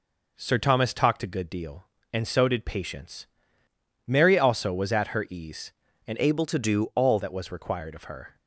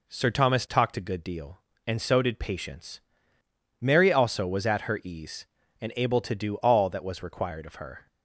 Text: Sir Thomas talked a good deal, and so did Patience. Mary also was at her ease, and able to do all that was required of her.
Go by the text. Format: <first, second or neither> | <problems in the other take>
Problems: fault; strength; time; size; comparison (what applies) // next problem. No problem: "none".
second | changes voice from "able" to "all"; from 6.1 to 7.1 s; 1.0 s long